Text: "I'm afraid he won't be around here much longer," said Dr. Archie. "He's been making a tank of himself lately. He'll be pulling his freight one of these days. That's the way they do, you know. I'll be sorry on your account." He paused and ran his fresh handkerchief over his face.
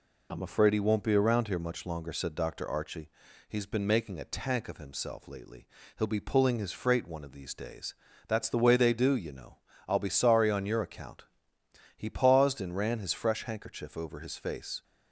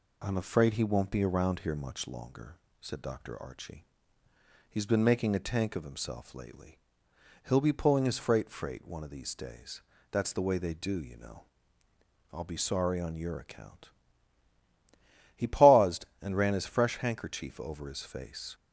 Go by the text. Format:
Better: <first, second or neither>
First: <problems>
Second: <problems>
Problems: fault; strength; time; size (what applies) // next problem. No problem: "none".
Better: first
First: none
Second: says "freight" twice; at 8.4 s